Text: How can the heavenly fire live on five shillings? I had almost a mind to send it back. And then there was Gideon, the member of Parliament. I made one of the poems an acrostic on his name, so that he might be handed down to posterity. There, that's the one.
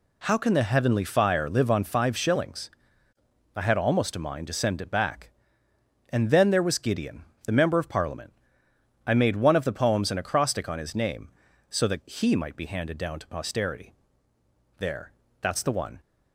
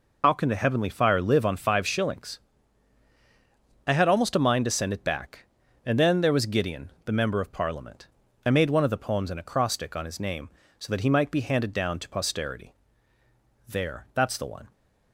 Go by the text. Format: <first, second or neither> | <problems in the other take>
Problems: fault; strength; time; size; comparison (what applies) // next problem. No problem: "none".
first | loses the start of "How"; at 0.2 s; 85 ms